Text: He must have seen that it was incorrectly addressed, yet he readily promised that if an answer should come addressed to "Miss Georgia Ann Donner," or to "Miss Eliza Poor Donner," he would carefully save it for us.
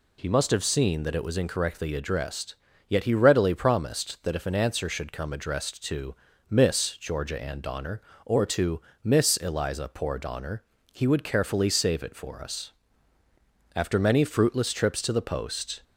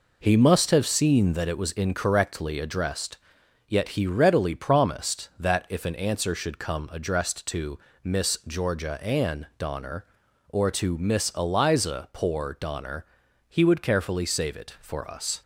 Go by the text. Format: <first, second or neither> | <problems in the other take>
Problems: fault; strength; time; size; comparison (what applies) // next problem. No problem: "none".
second | pauses between "to" and "Miss"; slight; at 6.1 s; 0.36 s long; slight in the second // pauses between "to" and "Miss"; slight; at 8.8 s; 0.20 s long // goes on to say "After many fruitless trips to the post"; strong; from 13.7 s on; 2.0 s long